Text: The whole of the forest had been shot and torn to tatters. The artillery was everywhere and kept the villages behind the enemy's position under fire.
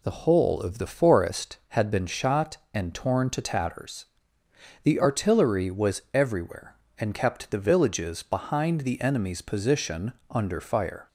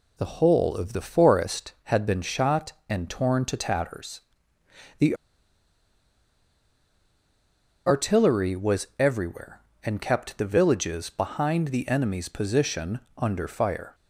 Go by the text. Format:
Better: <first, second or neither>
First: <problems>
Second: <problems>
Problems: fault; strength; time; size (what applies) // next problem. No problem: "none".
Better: first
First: pauses between "position" and "under"; slight; at 10.1 s; 0.16 s long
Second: pauses between "The" and "artillery"; strong; at 5.1 s; 2.7 s long // pauses between "position" and "under"; slight; at 13.0 s; 0.16 s long